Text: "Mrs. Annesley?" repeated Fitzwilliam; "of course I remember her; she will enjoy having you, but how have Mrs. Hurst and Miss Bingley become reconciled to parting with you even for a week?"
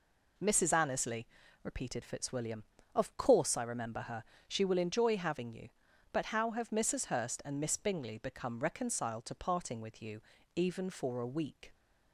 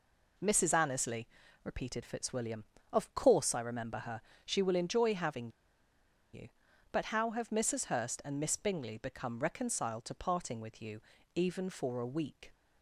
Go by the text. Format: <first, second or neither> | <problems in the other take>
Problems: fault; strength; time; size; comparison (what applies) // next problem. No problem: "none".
first | pauses between "having" and "you"; noticeable; at 5.4 s; 0.84 s long // pauses between "you" and "even"; slight; at 11.0 s; 0.34 s long; slight in the first